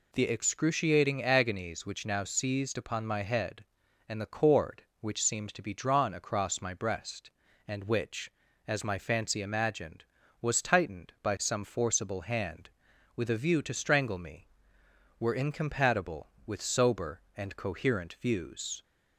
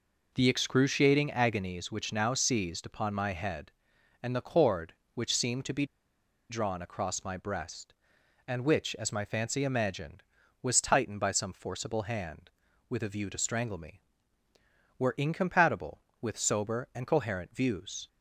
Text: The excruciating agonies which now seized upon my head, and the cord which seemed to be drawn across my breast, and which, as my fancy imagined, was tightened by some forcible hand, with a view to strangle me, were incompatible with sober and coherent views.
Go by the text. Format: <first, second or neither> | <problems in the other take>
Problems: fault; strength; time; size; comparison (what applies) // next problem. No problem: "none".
first | pauses between "be" and "drawn"; noticeable; at 5.8 s; 0.65 s long